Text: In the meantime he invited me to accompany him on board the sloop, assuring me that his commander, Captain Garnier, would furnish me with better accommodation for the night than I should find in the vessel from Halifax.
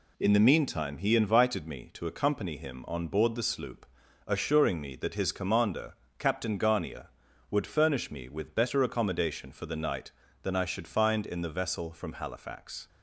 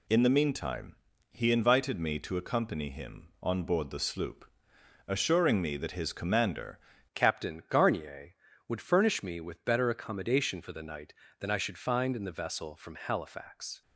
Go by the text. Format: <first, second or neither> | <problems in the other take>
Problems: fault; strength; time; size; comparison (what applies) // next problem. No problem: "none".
first | pauses between "meantime" and "he"; slight; at 0.9 s; 0.36 s long // changes voice at "Captain"; from 7.1 s on; 6.7 s long